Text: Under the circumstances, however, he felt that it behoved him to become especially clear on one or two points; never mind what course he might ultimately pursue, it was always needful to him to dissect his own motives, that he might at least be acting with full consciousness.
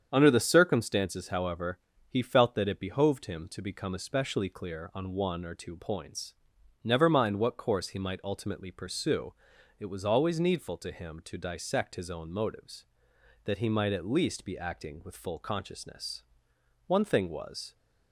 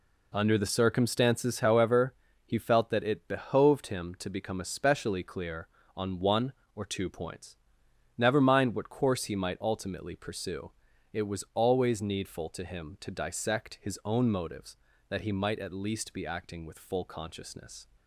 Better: second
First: starts louder than the rest; strong; until 1.1 s; 8 dB // goes on to say "One thing was"; noticeable; from 16.8 s on; 0.88 s long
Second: none

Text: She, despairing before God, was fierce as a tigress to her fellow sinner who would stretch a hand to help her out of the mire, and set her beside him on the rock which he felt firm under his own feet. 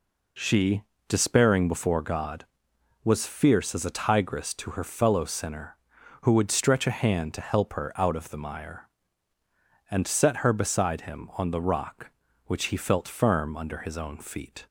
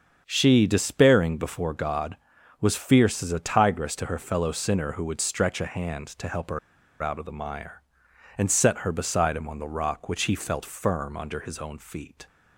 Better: first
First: none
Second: starts louder than the rest; until 1.2 s; 7 dB // pauses between "her" and "out"; at 6.5 s; 0.43 s long

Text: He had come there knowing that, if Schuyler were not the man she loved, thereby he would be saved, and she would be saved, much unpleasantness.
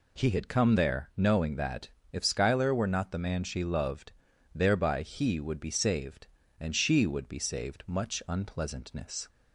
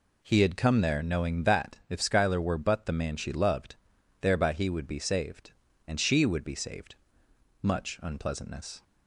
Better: first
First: none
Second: says "but" for "not"; at 2.5 s

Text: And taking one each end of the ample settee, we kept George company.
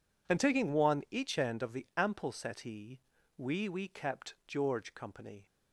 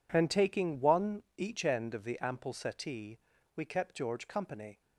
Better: second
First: says "we" twice; at 3.6 s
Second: none

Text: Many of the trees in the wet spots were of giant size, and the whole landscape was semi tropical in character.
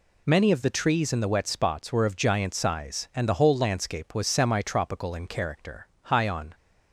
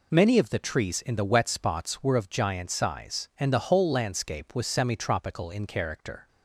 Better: second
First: goes on to say "High on"; from 6.0 s on; 0.52 s long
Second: none

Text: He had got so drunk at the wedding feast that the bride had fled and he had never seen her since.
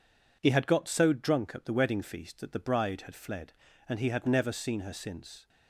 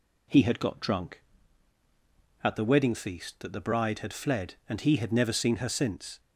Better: first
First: none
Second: skips "so"; at 0.7 s

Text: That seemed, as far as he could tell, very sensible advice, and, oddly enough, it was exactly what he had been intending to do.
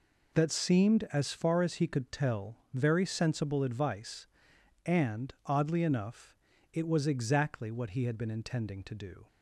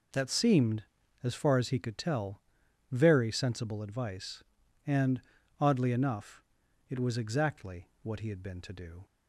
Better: first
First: none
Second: skips "intending"; at 8.6 s

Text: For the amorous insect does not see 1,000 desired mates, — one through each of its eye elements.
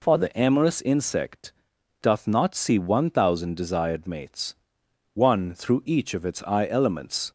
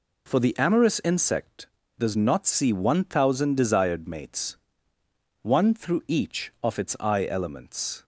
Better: second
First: says "doth" for "does"; at 2.0 s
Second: none

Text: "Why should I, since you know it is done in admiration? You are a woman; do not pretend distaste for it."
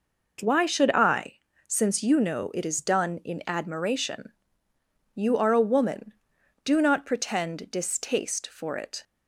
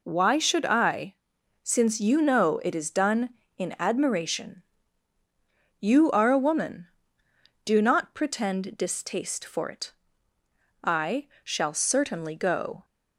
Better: first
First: none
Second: goes on to say "I shall certainly go"; strong; from 10.8 s on; 2.0 s long

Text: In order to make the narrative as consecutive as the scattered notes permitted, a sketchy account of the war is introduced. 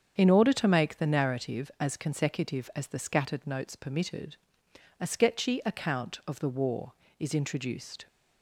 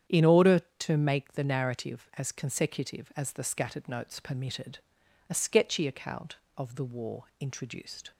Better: first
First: starts louder than the rest; strong; until 1.1 s; 7.5 dB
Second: starts louder than the rest; strong; until 1.2 s; 8.5 dB // skips "is"; at 7.3 s

